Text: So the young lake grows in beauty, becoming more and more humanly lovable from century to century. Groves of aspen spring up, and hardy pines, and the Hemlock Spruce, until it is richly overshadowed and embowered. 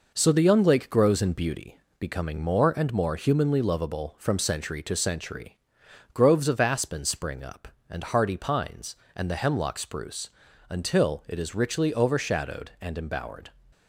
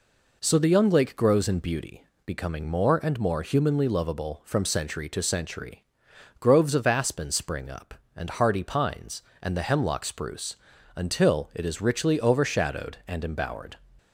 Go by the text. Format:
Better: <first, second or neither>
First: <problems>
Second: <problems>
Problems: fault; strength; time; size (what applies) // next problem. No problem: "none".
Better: second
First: gets quieter; noticeable; throughout; 4.5 dB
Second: none